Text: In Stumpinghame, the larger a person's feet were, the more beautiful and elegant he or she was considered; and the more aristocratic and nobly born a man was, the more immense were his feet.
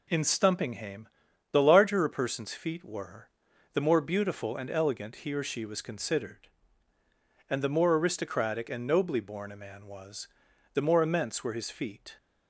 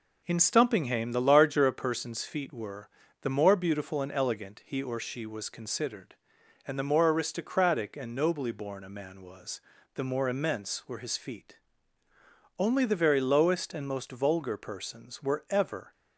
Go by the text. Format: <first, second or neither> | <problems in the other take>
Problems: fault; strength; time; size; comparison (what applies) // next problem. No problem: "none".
first | goes on to say "Only the very lowest and most vulgar persons were ever"; strong; from 12.5 s on; 3.3 s long